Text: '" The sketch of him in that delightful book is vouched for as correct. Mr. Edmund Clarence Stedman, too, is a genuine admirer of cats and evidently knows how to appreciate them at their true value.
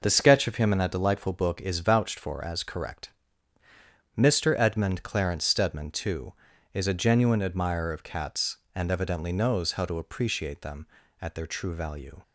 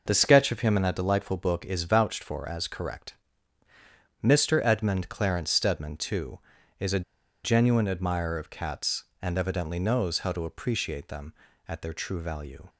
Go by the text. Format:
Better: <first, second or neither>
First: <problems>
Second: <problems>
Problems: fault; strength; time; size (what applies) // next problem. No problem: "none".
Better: first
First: none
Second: pauses between "a" and "genuine"; at 7.0 s; 0.42 s long